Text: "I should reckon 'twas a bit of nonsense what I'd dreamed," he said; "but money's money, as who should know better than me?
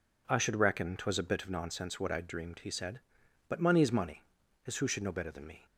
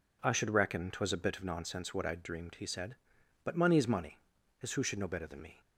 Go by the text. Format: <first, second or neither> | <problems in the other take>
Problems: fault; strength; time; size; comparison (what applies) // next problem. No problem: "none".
neither | none